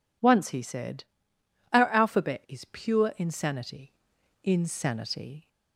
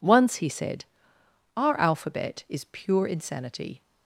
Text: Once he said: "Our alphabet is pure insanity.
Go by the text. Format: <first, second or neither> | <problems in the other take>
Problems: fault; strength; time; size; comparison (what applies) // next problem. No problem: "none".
second | says "insanity" twice; at 4.4 s